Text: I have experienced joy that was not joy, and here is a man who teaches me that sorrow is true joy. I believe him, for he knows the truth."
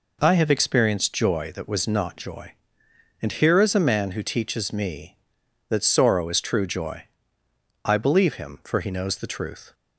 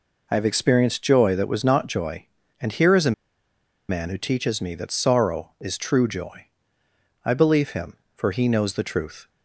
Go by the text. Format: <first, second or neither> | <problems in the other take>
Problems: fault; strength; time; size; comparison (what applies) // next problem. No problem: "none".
first | pauses between "a" and "man"; noticeable; at 3.1 s; 0.77 s long